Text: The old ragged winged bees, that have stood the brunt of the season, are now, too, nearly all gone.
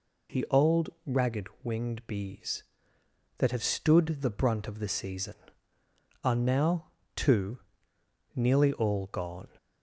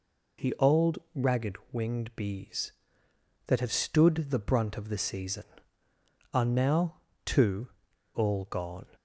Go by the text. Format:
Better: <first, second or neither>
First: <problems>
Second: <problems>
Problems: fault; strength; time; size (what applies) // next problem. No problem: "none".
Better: first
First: pauses between "ragged" and "winged"; slight; at 1.4 s; 0.16 s long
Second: pauses between "ragged" and "winged"; slight; at 1.5 s; 0.16 s long // skips "nearly"; at 7.9 s